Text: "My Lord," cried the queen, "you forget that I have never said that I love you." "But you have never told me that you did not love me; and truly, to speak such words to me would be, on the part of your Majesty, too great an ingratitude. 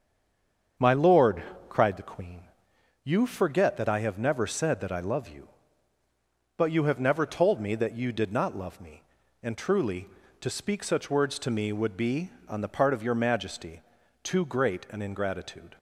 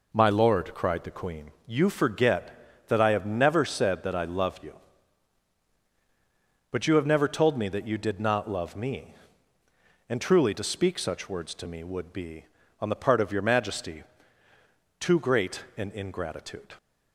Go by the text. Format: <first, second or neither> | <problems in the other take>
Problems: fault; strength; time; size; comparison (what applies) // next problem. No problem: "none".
second | stays silent before the first word; slight; until 0.7 s; 0.7 s long // starts louder than the rest; strong; until 2.0 s; 7.5 dB